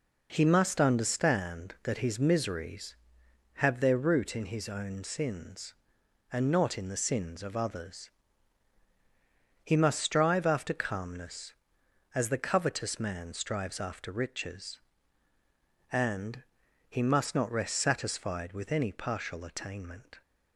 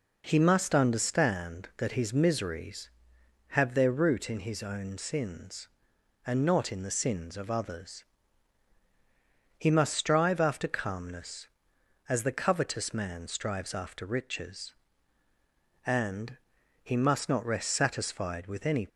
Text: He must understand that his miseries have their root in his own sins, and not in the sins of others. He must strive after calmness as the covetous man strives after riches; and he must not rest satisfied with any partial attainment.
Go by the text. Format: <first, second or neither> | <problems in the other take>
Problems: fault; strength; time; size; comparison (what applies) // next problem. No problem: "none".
first | pauses between "and" and "he"; noticeable; at 16.3 s; 0.46 s long; noticeable in the first // stops before "partial attainment"; at 18.8 s